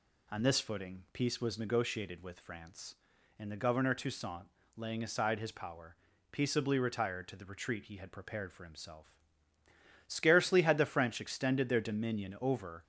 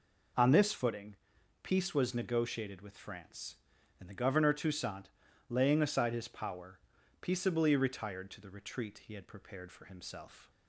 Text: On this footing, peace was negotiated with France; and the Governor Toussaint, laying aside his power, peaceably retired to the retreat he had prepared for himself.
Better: second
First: goes on to say "Scarcely had the French extended their dominion over"; strong; from 10.0 s on; 2.7 s long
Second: none

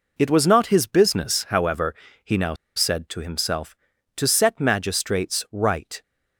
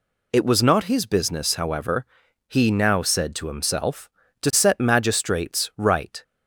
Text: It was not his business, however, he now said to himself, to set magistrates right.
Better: second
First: pauses between "now" and "said"; slight; at 2.5 s; 0.21 s long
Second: none

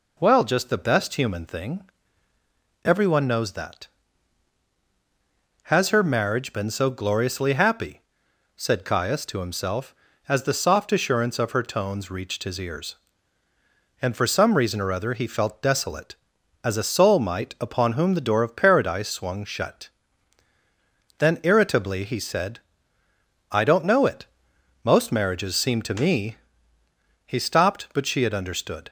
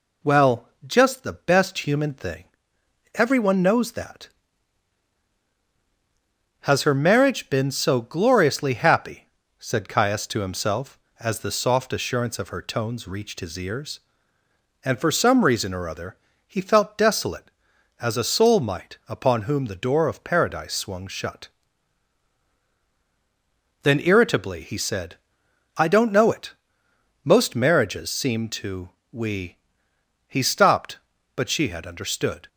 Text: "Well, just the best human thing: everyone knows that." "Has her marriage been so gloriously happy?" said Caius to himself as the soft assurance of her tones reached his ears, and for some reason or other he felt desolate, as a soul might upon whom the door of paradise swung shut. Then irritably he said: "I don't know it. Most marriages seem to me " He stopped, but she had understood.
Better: first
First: none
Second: pauses between "other" and "he"; slight; at 16.1 s; 0.28 s long // says "we" for "me"; at 29.1 s

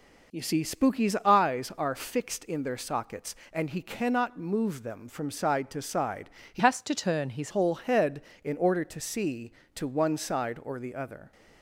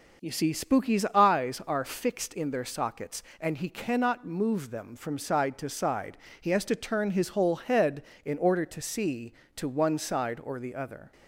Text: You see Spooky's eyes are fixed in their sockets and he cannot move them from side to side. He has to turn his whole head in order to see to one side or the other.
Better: second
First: changes voice from "has" to "his"; from 6.5 to 7.5 s; 1.0 s long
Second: none

